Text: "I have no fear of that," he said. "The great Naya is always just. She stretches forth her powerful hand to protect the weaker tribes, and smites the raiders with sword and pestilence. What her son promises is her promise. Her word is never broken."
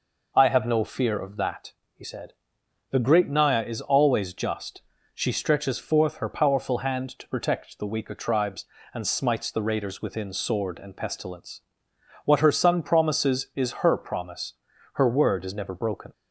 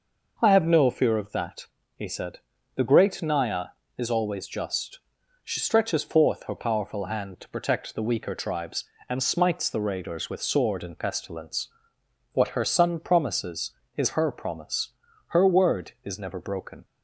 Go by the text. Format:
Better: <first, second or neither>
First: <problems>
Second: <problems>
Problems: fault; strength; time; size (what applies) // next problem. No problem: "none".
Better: second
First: says "within" for "with"; at 10.0 s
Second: none